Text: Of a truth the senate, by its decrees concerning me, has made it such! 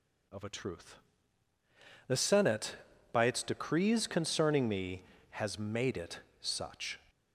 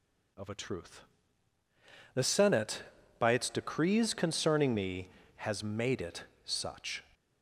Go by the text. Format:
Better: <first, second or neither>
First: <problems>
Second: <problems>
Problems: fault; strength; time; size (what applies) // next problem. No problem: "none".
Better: neither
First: pauses between "truth" and "the"; at 0.9 s; 1.1 s long // pauses between "it" and "such"; slight; at 6.1 s; 0.22 s long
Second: pauses between "truth" and "the"; at 1.0 s; 1.1 s long // pauses between "it" and "such"; slight; at 6.2 s; 0.22 s long